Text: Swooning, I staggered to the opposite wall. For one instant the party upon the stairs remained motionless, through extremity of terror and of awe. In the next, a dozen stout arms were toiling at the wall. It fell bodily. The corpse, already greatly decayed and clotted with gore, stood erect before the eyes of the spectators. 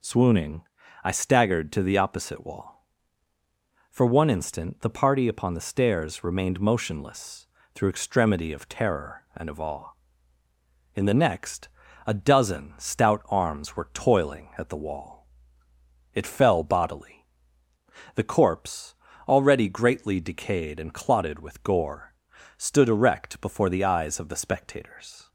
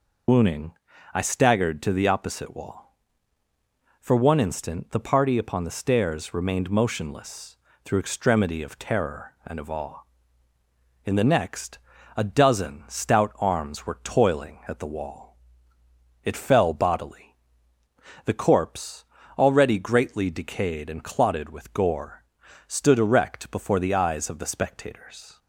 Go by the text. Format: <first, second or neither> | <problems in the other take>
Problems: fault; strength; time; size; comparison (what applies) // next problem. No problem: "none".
first | loses the start of "Swooning"; at 0.2 s; 150 ms